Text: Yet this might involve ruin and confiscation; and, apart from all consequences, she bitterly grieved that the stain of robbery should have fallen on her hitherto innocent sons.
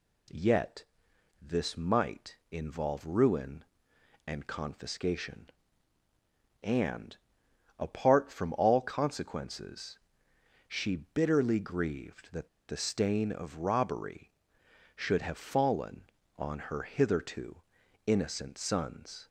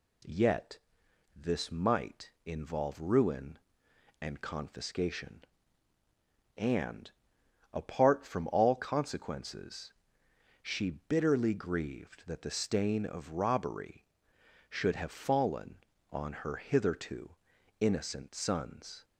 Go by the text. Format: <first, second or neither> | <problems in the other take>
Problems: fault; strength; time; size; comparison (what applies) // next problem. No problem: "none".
second | pauses between "Yet" and "this"; noticeable; at 0.8 s; 0.58 s long; noticeable in the second // pauses between "that" and "the"; slight; at 12.4 s; 0.21 s long // pauses between "hitherto" and "innocent"; noticeable; at 17.6 s; 0.46 s long; noticeable in the second